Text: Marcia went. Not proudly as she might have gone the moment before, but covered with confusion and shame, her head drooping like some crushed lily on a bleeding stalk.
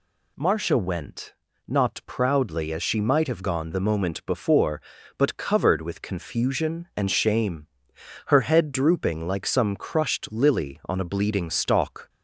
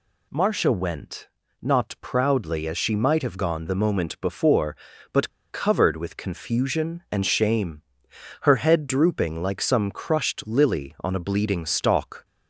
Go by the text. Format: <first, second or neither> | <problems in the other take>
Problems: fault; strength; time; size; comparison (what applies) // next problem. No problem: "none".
first | pauses between "but" and "covered"; slight; at 5.2 s; 0.22 s long